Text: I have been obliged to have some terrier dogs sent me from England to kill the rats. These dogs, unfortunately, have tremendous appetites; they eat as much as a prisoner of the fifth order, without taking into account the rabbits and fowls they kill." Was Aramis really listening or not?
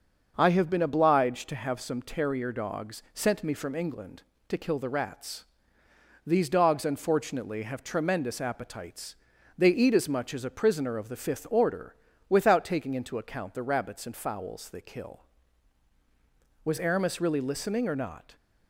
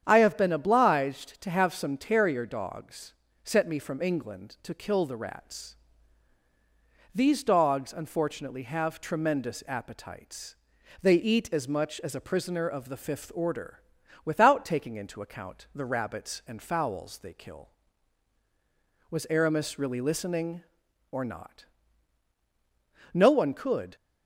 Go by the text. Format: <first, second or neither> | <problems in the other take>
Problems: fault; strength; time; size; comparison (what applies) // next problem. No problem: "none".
first | starts louder than the rest; strong; until 1.0 s; 8.5 dB; also in the first // pauses between "dogs" and "sent"; slight; at 3.1 s; 0.32 s long // goes on to say "No one could"; noticeable; from 23.1 s on; 0.82 s long